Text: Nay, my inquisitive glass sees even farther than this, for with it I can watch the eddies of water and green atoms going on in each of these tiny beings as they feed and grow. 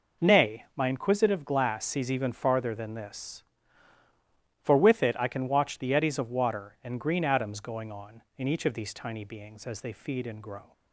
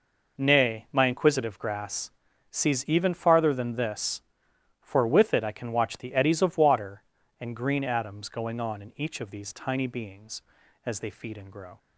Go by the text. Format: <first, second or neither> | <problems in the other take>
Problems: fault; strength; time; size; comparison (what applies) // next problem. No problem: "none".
first | says "grass" for "glass"; at 1.5 s